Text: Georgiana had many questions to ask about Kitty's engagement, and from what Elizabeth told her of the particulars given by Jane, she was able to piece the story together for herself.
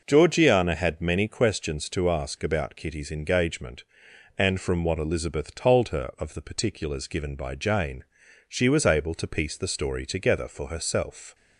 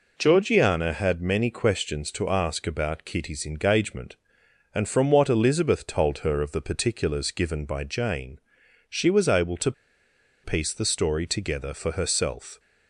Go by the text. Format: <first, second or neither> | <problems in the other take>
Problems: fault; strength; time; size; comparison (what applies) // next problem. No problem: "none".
first | pauses between "to" and "piece"; noticeable; at 9.7 s; 0.71 s long